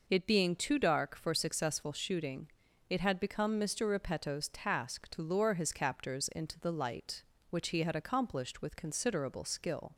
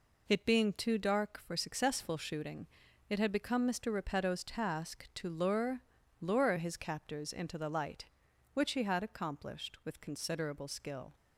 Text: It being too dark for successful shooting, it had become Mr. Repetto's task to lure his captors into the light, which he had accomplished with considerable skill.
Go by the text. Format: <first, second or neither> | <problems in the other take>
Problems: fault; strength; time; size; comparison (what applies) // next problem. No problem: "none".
first | says "lure" twice; at 6.1 s